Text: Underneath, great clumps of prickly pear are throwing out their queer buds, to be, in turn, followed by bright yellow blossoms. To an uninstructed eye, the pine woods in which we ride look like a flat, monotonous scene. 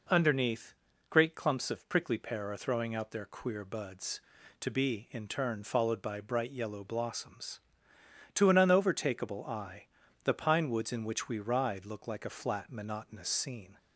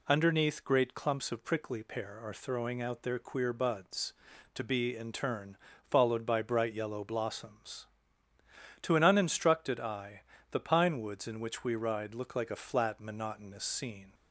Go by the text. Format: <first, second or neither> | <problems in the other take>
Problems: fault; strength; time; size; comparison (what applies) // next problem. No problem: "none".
second | says "unovertakable" for "uninstructed"; at 8.5 s